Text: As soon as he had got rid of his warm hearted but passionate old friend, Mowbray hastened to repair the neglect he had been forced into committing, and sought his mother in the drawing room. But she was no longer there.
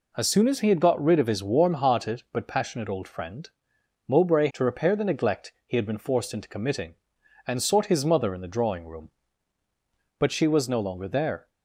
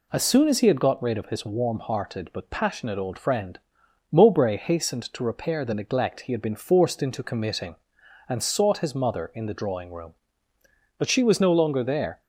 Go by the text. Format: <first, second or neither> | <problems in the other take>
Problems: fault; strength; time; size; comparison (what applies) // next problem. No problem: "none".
second | skips "hastened"; at 4.5 s